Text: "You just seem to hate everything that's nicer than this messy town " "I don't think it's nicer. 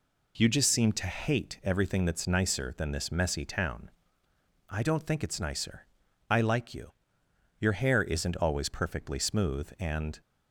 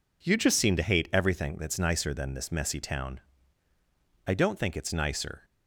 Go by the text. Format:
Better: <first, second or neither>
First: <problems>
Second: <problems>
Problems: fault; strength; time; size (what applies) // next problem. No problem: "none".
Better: second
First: goes on to say "I like you your hair isn't always perfectly smooth and"; strong; from 6.2 s on; 3.9 s long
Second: none